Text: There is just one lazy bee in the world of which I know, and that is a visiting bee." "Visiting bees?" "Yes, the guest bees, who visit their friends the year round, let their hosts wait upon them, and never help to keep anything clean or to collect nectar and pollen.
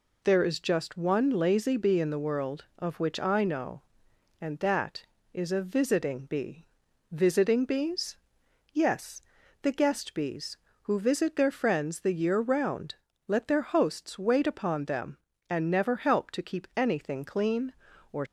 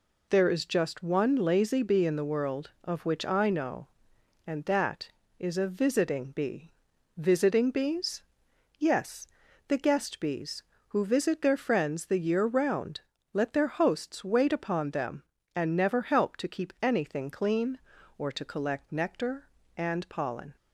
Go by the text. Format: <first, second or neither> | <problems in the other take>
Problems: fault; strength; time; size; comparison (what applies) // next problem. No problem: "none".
second | stops before "to collect nectar and pollen"; at 18.2 s